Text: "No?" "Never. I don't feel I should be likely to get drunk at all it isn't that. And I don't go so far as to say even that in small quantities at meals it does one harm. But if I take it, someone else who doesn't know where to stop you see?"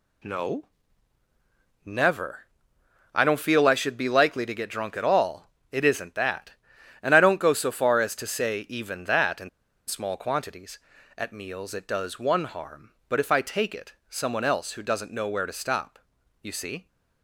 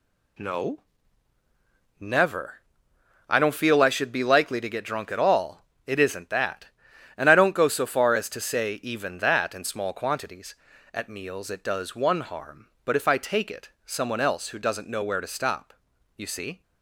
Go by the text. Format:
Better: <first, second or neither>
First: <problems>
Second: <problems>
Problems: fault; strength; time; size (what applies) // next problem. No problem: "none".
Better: second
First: pauses between "all" and "it"; slight; at 5.5 s; 0.18 s long // pauses between "in" and "small"; at 9.4 s; 0.39 s long // pauses between "stop" and "you"; at 15.9 s; 0.42 s long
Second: pauses between "all" and "it"; slight; at 5.6 s; 0.18 s long // pauses between "stop" and "you"; at 15.7 s; 0.42 s long